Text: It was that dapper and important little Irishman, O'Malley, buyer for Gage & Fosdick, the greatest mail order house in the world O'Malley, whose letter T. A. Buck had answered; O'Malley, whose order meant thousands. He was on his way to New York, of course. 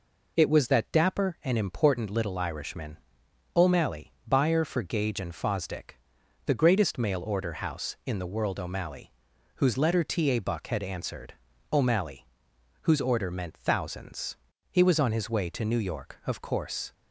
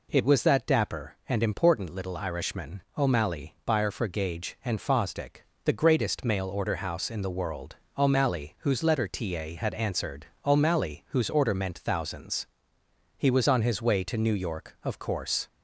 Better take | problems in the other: first | pauses between "world" and "O'Malley"; slight; at 7.7 s; 0.20 s long // skips "Buck"; at 9.5 s

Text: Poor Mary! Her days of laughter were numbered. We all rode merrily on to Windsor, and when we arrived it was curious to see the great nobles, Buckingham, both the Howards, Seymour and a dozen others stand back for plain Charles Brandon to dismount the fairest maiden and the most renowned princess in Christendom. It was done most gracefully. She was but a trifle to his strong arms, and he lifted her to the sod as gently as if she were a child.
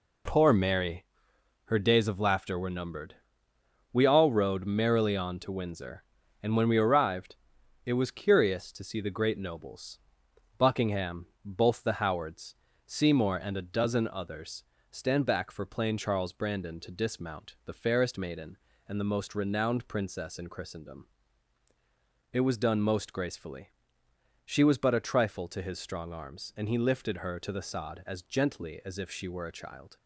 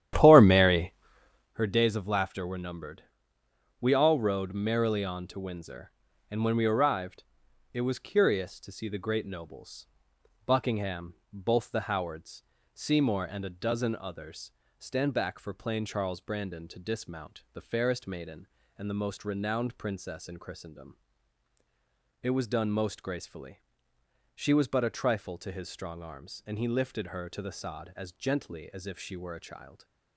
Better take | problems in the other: first | starts louder than the rest; strong; until 1.6 s; 11.5 dB // pauses between "arrived" and "it"; noticeable; at 7.2 s; 0.50 s long; noticeable in the first // pauses between "others" and "stand"; slight; at 14.5 s; 0.26 s long; slight in the first

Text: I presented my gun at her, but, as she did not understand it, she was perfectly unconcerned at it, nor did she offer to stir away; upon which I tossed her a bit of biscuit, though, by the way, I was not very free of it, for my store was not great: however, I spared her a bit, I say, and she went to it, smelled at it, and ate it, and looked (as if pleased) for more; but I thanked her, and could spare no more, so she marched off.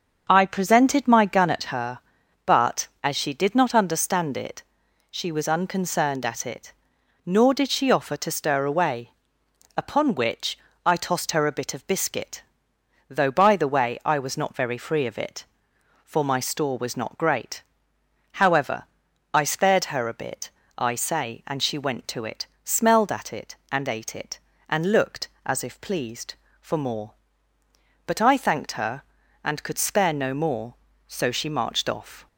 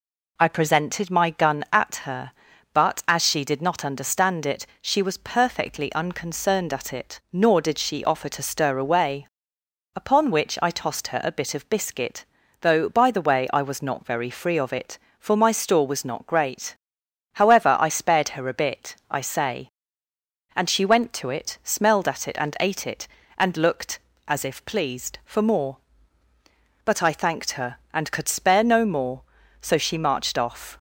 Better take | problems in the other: second | starts louder than the rest; until 1.2 s; 7 dB // skips "perfectly"; at 5.4 s // pauses between "which" and "I"; slight; at 10.5 s; 0.26 s long

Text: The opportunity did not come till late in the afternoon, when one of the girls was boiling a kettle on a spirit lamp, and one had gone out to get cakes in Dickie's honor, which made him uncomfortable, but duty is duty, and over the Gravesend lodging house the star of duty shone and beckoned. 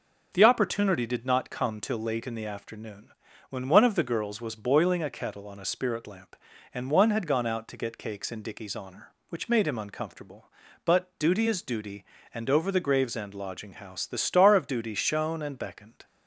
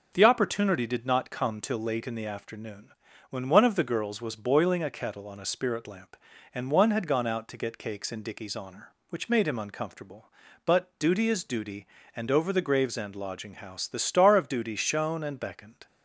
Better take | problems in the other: neither | none

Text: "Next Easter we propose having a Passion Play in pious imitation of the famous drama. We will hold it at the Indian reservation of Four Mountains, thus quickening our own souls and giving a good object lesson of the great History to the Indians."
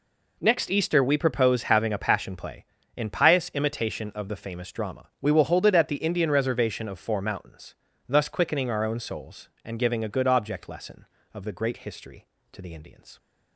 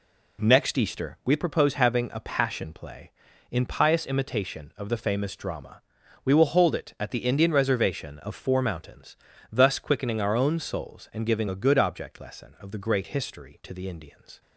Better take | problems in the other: neither | none

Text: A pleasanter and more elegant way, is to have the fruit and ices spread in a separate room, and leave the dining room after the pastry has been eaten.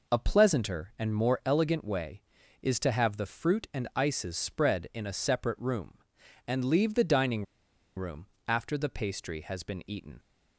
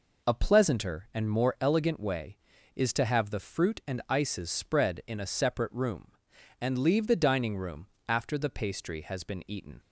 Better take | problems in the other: second | pauses between "dining" and "room"; noticeable; at 7.4 s; 0.52 s long // pauses between "room" and "after"; slight; at 8.2 s; 0.18 s long; slight in the second

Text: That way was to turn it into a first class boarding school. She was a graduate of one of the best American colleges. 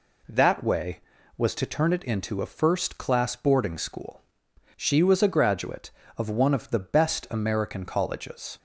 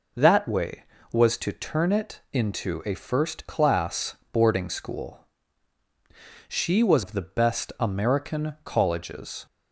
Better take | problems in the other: first | pauses between "class" and "boarding"; slight; at 4.1 s; 0.16 s long // skips "a graduate of one"; at 7.0 s

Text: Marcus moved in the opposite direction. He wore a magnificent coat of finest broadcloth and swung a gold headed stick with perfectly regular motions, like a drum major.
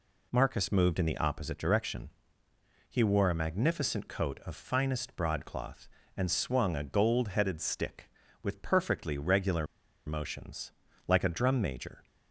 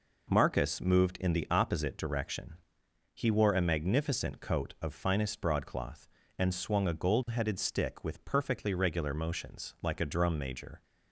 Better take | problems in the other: second | pauses between "regular" and "motions"; at 9.6 s; 0.40 s long

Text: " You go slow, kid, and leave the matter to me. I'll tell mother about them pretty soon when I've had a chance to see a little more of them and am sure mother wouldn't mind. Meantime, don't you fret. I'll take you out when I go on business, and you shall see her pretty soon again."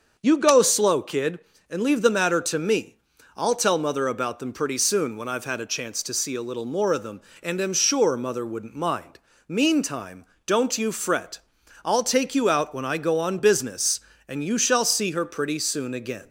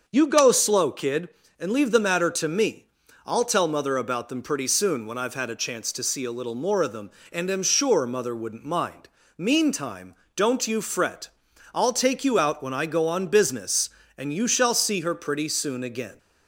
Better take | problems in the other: neither | starts louder than the rest; the same in both

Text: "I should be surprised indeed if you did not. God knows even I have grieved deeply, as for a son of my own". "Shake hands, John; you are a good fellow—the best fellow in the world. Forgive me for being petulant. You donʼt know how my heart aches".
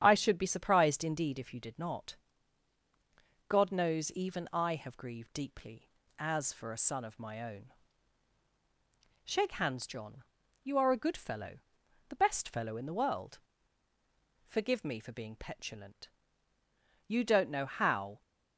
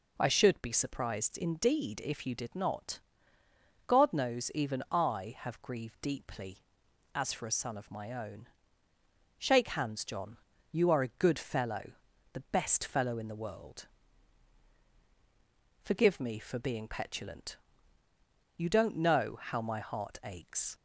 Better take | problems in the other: second | starts louder than the rest; strong; until 1.0 s; 9.5 dB // stops before "my heart aches"; at 18.2 s

